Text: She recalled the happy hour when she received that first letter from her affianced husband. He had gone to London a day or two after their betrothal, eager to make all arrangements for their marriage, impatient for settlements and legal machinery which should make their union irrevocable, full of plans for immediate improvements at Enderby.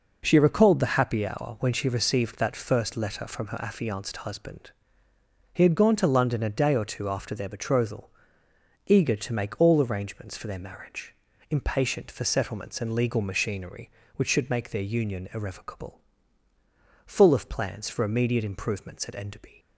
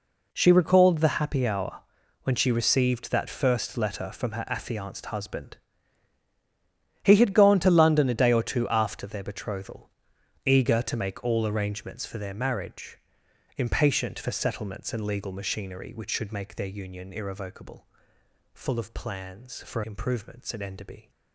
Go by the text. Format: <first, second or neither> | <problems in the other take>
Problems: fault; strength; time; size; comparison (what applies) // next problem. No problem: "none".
first | pauses between "hour" and "when"; at 1.8 s; 0.42 s long // skips "immediate"; at 19.8 s